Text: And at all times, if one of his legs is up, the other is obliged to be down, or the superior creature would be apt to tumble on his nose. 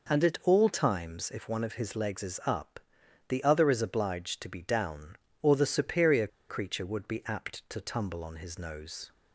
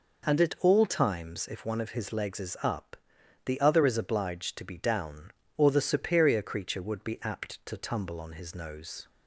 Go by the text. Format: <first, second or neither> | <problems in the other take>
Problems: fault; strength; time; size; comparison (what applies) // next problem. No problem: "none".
second | pauses between "superior" and "creature"; slight; at 6.2 s; 0.21 s long